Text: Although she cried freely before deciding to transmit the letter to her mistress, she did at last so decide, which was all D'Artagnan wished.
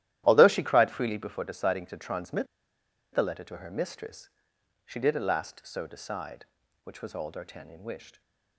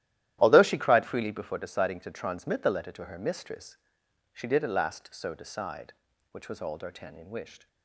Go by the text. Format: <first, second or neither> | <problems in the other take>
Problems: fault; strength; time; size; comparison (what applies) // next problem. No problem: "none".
second | starts louder than the rest; strong; until 1.2 s; 13 dB; strong in the second // pauses between "transmit" and "the"; noticeable; at 2.4 s; 0.68 s long